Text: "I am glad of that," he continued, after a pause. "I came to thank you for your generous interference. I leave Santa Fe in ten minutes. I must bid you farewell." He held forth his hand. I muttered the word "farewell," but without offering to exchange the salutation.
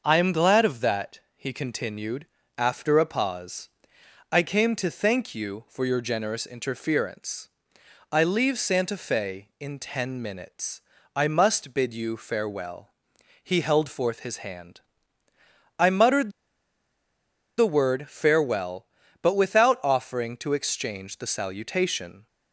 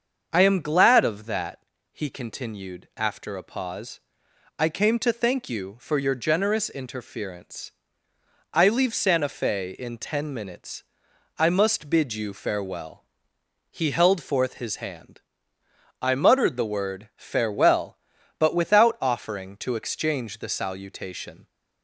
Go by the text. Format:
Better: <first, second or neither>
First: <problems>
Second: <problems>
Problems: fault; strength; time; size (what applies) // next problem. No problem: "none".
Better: second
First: starts louder than the rest; until 1.0 s; 6 dB // pauses between "muttered" and "the"; strong; at 16.3 s; 1.2 s long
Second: starts louder than the rest; until 1.3 s; 7 dB